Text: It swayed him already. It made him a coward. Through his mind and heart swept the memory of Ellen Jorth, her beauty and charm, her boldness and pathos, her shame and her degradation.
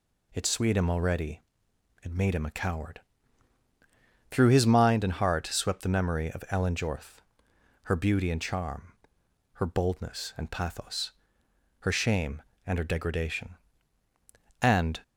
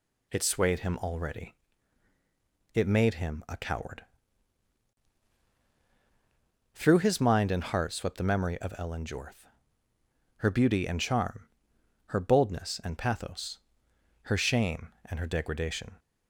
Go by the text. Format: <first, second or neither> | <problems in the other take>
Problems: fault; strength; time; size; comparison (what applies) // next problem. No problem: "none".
second | goes on to say "And"; slight; from 14.6 s on; 0.40 s long